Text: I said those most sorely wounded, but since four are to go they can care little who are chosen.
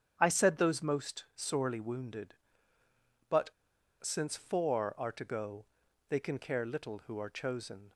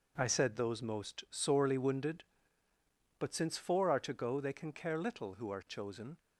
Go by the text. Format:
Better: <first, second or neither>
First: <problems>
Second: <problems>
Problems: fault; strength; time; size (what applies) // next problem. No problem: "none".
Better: second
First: starts louder than the rest; strong; until 1.2 s; 9 dB // pauses between "but" and "since"; noticeable; at 3.5 s; 0.50 s long // pauses between "go" and "they"; at 5.6 s; 0.42 s long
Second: none